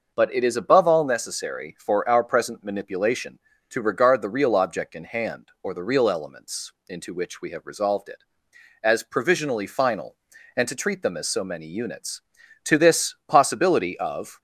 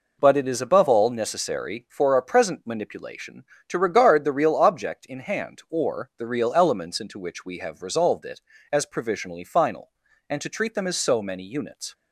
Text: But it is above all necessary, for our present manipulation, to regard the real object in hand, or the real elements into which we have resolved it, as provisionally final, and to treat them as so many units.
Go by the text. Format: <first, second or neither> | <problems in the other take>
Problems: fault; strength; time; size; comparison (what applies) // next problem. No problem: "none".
second | pauses between "elements" and "into"; slight; at 6.7 s; 0.16 s long // goes on to say "To this possibility of"; strong; from 12.6 s on; 1.7 s long